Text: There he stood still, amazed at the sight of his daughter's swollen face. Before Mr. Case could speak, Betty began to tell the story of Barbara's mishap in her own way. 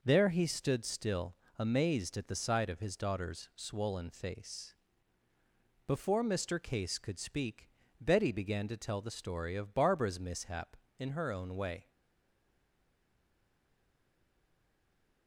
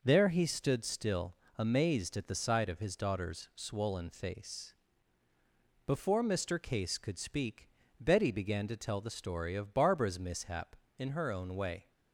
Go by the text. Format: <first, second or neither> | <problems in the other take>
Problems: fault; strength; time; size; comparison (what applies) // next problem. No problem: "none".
second | stays silent after the last word; strong; from 11.9 s on; 3.3 s long